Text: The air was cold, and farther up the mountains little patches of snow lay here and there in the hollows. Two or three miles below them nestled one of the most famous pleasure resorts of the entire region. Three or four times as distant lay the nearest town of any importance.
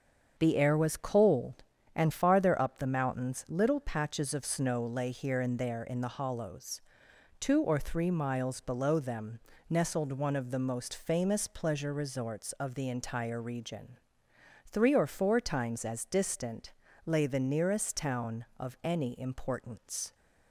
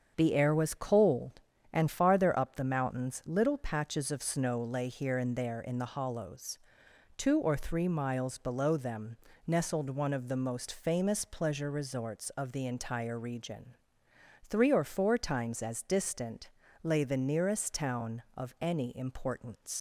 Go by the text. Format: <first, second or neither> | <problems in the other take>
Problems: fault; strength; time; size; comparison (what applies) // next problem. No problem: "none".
first | starts louder than the rest; strong; until 1.1 s; 7.5 dB; strong in the first // pauses between "them" and "nestled"; slight; at 9.1 s; 0.30 s long; slight in the first // pauses between "distant" and "lay"; slight; at 16.5 s; 0.32 s long; slight in the first // leaves "importance" unfinished; at 19.7 s; 125 ms